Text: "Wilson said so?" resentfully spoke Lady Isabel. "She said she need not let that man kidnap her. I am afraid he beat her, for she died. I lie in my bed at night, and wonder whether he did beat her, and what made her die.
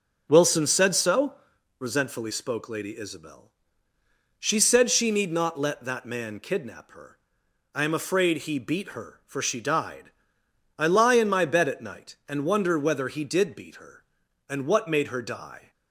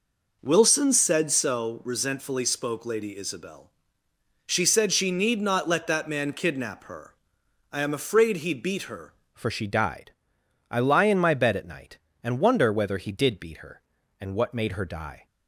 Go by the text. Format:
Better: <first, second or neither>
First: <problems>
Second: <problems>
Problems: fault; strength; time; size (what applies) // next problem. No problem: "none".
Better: first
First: none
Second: changes voice at "for"; from 9.3 s on; 5.9 s long